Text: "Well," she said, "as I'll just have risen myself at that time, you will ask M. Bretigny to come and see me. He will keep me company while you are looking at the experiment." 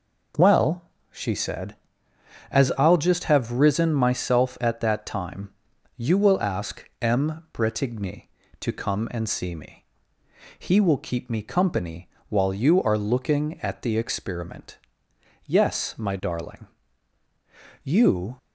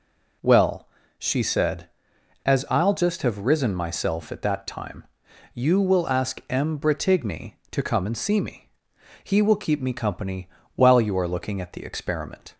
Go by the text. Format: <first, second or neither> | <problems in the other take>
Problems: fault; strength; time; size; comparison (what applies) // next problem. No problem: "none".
second | pauses between "company" and "while"; slight; at 12.0 s; 0.18 s long; slight in the second // goes on to say "Yes my darling You"; strong; from 15.4 s on; 2.9 s long